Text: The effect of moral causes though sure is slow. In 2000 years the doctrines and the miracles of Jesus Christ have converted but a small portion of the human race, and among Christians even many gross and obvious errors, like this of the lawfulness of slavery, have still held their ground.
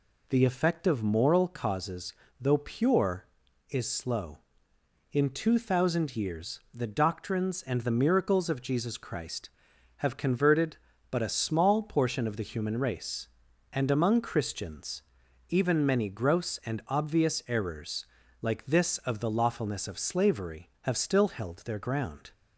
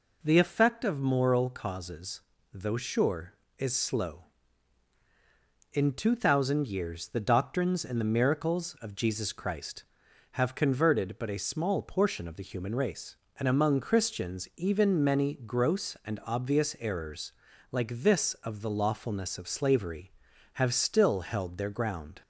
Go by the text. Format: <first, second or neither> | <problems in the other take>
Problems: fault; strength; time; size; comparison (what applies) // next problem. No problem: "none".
second | pauses between "causes" and "though"; slight; at 2.1 s; 0.28 s long; slight in the second // says "pure" for "sure"; at 2.5 s // pauses between "Christians" and "even"; noticeable; at 15.0 s; 0.46 s long